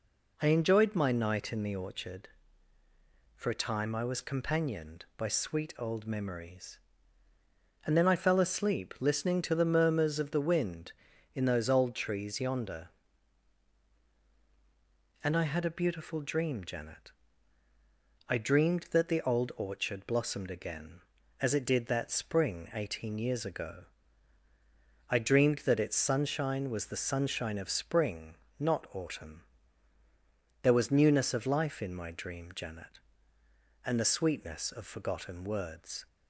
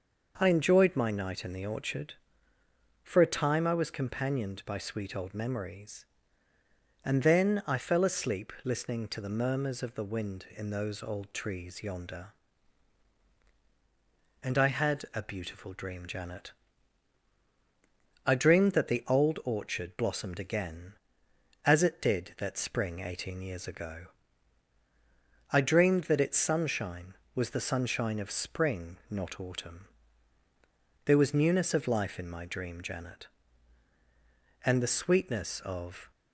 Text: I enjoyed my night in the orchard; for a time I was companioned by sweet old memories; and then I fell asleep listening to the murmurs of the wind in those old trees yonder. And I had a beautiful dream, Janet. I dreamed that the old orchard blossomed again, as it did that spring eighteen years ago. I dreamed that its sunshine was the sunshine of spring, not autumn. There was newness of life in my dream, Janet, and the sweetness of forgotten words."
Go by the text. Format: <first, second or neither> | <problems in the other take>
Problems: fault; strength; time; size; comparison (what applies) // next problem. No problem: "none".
first | starts louder than the rest; noticeable; until 1.3 s; 6 dB // stops before "forgotten words"; at 36.1 s